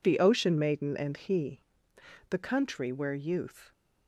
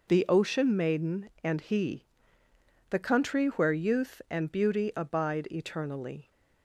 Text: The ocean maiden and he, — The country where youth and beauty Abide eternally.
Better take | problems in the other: second | stops before "and beauty Abide eternally"; at 3.7 s

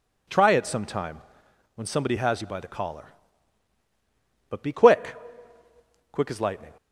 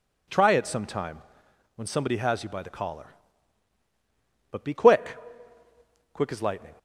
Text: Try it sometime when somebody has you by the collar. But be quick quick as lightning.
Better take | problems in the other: neither | pauses between "sometime" and "when"; noticeable; the same in both // pauses between "quick" and "quick"; noticeable; the same in both

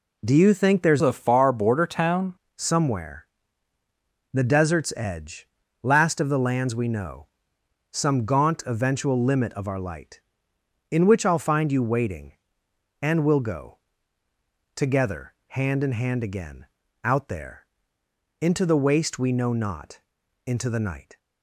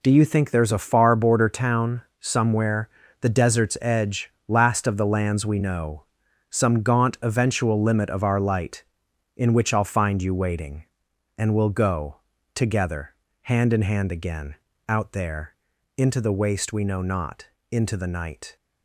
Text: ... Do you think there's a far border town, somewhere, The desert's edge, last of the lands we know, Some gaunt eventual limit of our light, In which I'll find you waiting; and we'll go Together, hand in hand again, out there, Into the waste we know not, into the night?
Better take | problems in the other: second | changes voice from "a" to "town"; from 1.0 to 2.3 s; 1.3 s long // pauses between "go" and "Together"; noticeable; at 13.7 s; 0.96 s long; also in the second

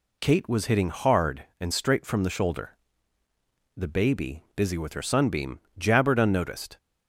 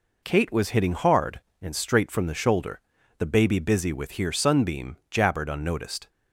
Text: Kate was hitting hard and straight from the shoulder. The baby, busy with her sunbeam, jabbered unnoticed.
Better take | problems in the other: first | says "here" for "her"; at 4.1 s

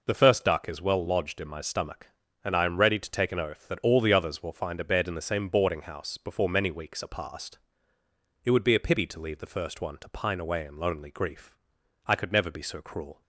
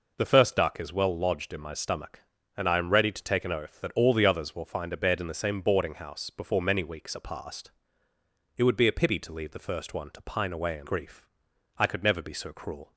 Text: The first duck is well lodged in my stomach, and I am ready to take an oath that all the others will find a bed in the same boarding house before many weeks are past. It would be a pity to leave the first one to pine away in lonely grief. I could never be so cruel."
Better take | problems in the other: first | skips "lonely"; at 10.8 s

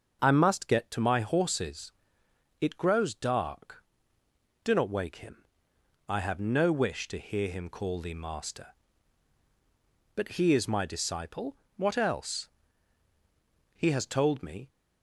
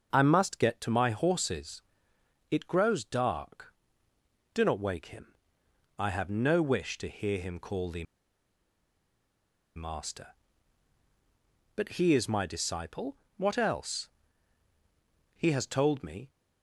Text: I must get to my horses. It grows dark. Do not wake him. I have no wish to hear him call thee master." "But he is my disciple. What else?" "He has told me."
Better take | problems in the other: first | starts louder than the rest; until 1.1 s; 6.5 dB; also in the first // pauses between "thee" and "master"; strong; at 8.0 s; 1.7 s long

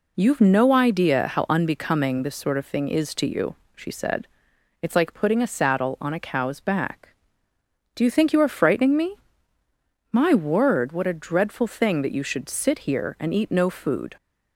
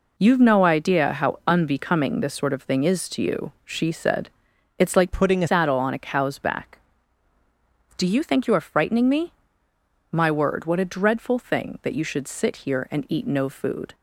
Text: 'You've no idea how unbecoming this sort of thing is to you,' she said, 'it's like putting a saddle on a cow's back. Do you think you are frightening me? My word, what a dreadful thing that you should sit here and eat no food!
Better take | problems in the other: first | changes voice from "putting" to "a"; from 5.1 to 5.4 s; 0.3 s long

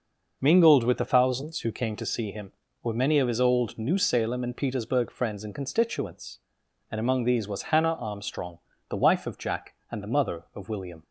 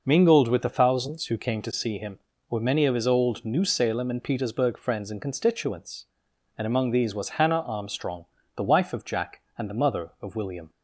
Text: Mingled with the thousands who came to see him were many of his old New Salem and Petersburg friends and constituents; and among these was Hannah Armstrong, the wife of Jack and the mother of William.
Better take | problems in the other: neither | none

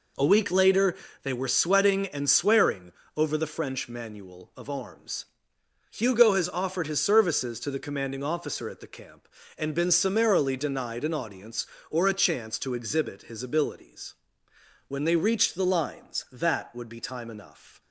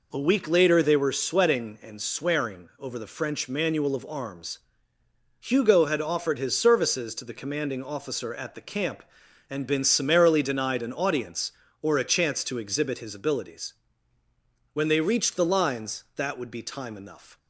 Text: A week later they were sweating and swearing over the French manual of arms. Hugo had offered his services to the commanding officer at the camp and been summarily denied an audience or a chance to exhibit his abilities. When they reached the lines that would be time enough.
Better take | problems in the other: second | pauses between "later" and "they"; slight; at 0.9 s; 0.28 s long // pauses between "swearing" and "over"; slight; at 2.9 s; 0.24 s long // says "has" for "had"; at 6.3 s

